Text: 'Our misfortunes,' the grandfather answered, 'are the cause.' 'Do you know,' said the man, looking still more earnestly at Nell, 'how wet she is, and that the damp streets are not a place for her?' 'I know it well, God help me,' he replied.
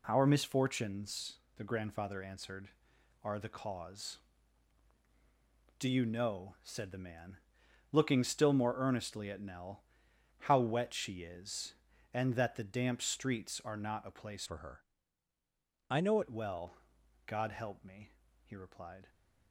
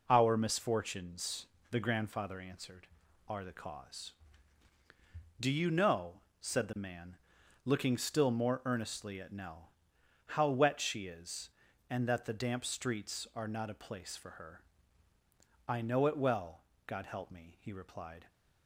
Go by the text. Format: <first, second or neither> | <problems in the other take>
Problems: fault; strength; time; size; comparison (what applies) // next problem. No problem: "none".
second | changes voice from "for" to "know"; from 14.4 to 16.1 s; 1.7 s long